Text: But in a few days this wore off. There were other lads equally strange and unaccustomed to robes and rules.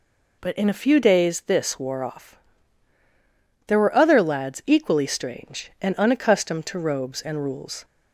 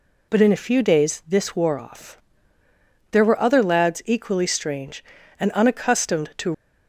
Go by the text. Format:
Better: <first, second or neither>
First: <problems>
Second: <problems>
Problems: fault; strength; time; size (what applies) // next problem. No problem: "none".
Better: first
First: none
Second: stops before "robes and rules"; at 6.5 s